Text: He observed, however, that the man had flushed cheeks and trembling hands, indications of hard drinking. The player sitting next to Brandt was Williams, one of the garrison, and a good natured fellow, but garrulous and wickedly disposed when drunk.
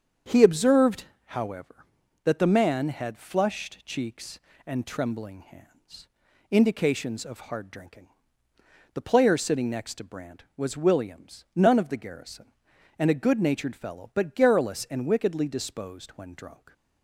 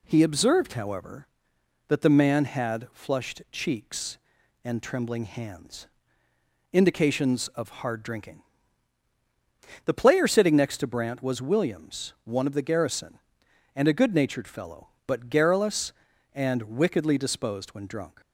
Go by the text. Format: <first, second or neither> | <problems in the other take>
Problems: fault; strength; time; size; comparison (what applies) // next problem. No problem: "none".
second | starts louder than the rest; strong; until 1.4 s; 7.5 dB // says "none" for "one"; at 11.5 s